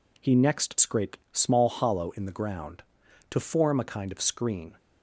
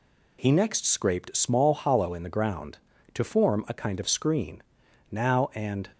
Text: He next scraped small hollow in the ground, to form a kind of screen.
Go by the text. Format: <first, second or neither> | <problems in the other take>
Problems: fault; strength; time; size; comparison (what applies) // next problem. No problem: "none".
first | goes on to say "Now and"; noticeable; from 5.1 s on; 0.78 s long